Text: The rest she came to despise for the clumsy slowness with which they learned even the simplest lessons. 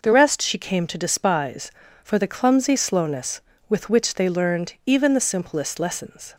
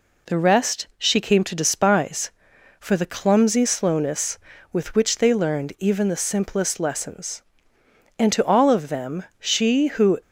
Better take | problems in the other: first | goes on to say "And to all of them she who"; strong; from 8.1 s on; 2.0 s long

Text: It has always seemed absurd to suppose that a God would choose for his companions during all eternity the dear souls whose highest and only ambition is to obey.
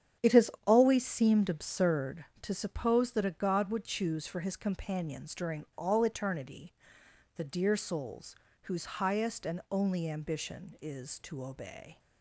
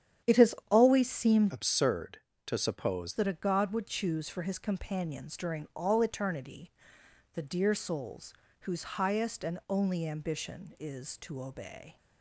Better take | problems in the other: first | starts louder than the rest; strong; until 1.4 s; 9.5 dB; strong in the first // pauses between "has" and "always"; slight; at 0.5 s; 0.16 s long; slight in the first // changes voice from "absurd" to "suppose"; from 1.5 to 3.1 s; 1.6 s long // pauses between "eternity" and "the"; noticeable; at 6.7 s; 0.62 s long; noticeable in the first // pauses between "souls" and "whose"; slight; at 8.3 s; 0.26 s long; slight in the first

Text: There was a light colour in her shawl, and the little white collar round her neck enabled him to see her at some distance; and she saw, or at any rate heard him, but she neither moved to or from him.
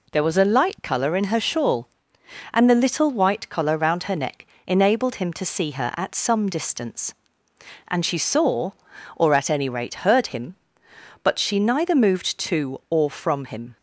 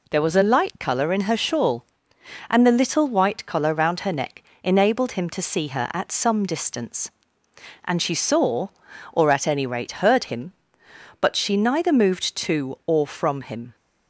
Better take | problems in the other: neither | pauses between "neck" and "enabled"; slight; the same in both

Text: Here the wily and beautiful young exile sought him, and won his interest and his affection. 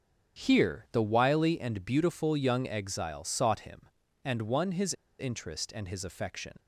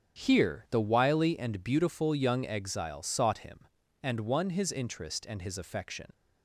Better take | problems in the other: second | starts louder than the rest; until 1.4 s; 7 dB; strong in the second // pauses between "his" and "interest"; slight; at 4.9 s; 0.26 s long

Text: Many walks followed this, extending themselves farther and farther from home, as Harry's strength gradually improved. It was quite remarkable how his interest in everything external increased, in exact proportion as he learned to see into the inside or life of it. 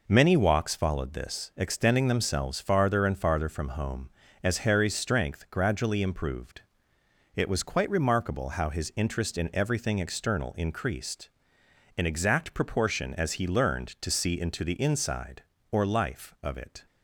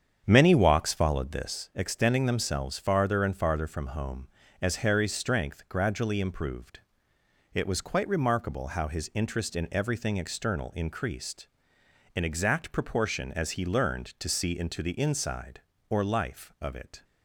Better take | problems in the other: first | starts louder than the rest; strong; until 1.6 s; 8 dB

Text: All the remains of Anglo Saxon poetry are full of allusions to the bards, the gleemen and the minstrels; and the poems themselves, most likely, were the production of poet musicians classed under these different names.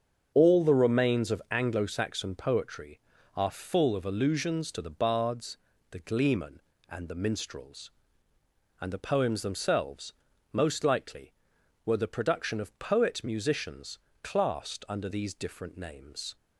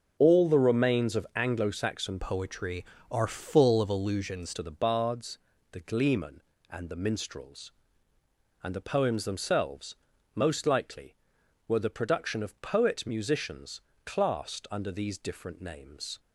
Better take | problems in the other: first | starts louder than the rest; until 1.2 s; 6 dB; strong in the first // changes voice from "poetry" to "allusions"; from 2.1 to 4.5 s; 2.4 s long // pauses between "musicians" and "classed"; slight; at 13.8 s; 0.24 s long; slight in the first

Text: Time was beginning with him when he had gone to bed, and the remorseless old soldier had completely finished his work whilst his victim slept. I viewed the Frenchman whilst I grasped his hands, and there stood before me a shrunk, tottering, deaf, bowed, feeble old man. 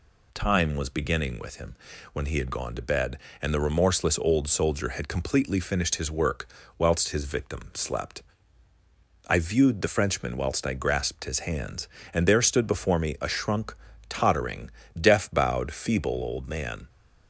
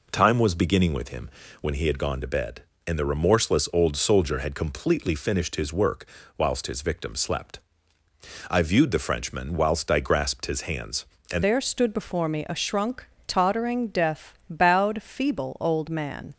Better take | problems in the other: first | pauses between "him" and "when"; slight; at 1.2 s; 0.32 s long; also in the first // pauses between "work" and "whilst"; slight; at 6.0 s; 0.32 s long; slight in the first // changes voice at "there"; from 11.4 s on; 4.9 s long

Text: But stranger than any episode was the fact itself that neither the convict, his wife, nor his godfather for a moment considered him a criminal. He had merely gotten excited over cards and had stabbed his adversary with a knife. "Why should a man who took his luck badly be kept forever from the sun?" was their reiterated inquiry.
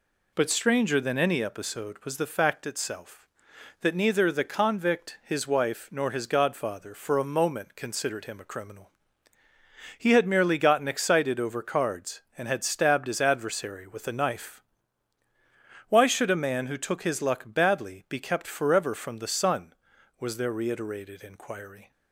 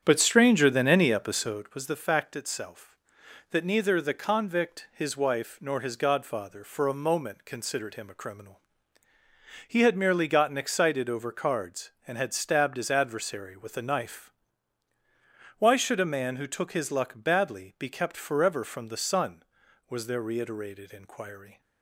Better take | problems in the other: first | starts louder than the rest; strong; until 1.7 s; 8.5 dB

